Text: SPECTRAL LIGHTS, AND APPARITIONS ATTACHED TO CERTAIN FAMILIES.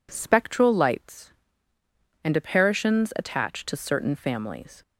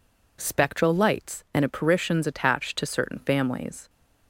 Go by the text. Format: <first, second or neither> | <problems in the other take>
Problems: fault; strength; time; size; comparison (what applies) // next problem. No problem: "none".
neither | none